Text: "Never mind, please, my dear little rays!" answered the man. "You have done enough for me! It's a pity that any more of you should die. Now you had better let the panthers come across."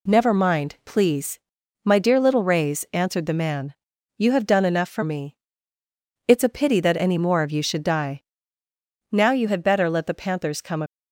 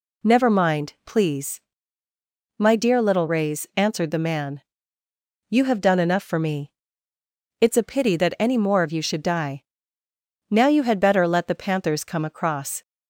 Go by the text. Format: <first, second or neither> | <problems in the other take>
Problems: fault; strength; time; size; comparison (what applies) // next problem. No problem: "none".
second | stops before "across"; at 10.8 s